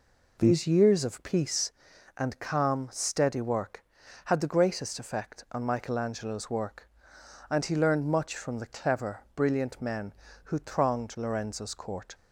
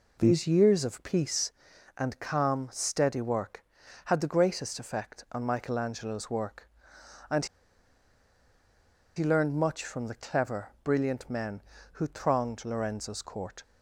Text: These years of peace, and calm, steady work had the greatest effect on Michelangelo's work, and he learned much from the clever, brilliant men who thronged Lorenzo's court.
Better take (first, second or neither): first